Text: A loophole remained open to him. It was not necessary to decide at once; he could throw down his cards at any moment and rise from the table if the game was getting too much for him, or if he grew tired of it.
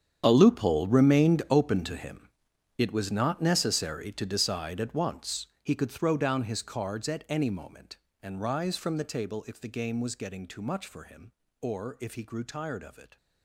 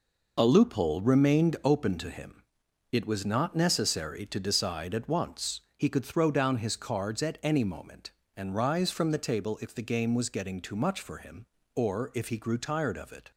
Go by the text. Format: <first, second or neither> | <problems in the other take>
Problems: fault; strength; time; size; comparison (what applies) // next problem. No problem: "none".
second | gets quieter; strong; throughout; 16 dB